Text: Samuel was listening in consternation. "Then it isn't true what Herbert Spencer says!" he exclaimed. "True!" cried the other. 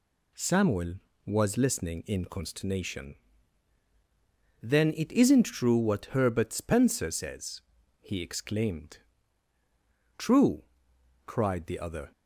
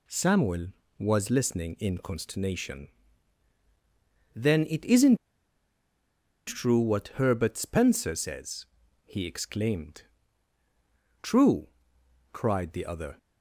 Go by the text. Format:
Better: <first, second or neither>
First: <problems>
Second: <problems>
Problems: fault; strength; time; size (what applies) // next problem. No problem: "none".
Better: first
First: none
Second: pauses between "isn't" and "true"; strong; at 5.1 s; 1.3 s long